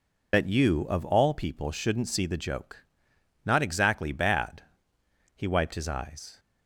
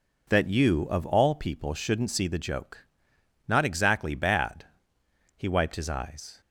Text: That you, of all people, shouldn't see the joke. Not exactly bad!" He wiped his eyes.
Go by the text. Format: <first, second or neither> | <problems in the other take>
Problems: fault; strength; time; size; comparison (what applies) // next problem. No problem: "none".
second | loses the start of "That"; at 0.3 s; 50 ms